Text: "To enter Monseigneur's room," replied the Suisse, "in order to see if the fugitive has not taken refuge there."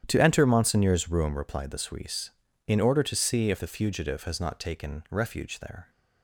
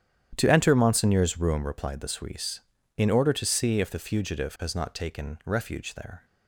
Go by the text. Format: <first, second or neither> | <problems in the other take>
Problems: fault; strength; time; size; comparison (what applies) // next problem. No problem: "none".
neither | starts louder than the rest; strong; the same in both